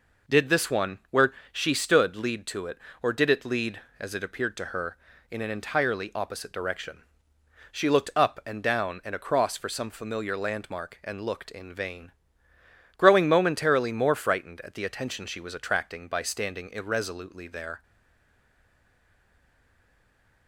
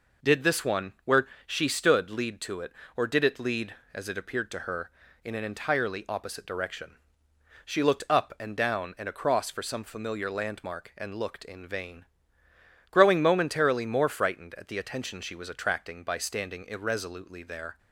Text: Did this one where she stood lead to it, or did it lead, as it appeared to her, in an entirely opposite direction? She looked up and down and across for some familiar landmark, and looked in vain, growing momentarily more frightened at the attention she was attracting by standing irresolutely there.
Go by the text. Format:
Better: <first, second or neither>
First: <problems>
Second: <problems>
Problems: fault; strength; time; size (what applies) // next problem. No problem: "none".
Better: second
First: pauses between "where" and "she"; slight; at 1.3 s; 0.20 s long // stays silent after the last word; strong; from 17.8 s on; 2.6 s long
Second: pauses between "where" and "she"; slight; at 1.2 s; 0.20 s long